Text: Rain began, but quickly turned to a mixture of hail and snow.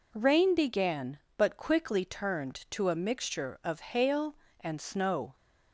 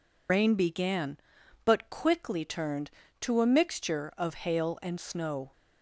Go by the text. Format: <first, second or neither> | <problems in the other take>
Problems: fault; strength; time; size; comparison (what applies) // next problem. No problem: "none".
first | loses the start of "Rain"; at 0.2 s; 80 ms